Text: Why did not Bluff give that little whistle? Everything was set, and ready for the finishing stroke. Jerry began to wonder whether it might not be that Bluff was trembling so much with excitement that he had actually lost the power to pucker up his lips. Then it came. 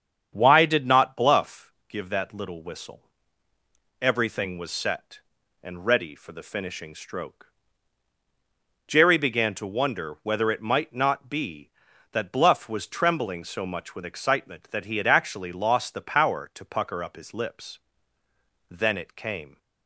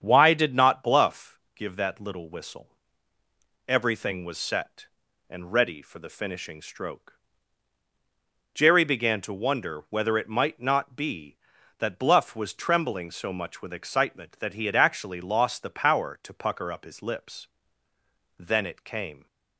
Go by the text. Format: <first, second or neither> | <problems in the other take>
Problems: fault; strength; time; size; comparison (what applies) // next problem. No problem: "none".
neither | starts louder than the rest; strong; the same in both // pauses between "Bluff" and "give"; slight; the same in both